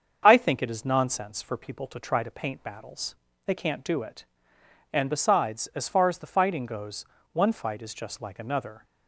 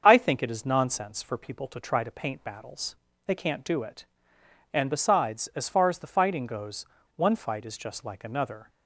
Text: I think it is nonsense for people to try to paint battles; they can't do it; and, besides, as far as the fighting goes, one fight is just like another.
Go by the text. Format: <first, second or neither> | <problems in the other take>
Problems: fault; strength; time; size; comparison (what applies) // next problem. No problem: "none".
neither | starts louder than the rest; the same in both